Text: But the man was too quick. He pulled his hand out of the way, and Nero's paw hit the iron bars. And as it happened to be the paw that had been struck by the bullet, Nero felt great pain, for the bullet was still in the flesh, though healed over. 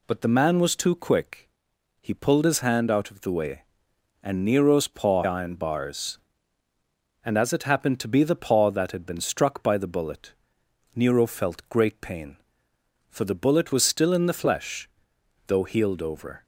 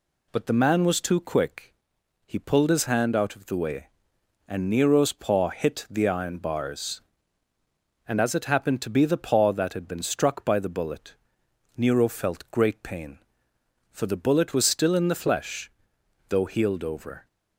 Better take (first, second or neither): second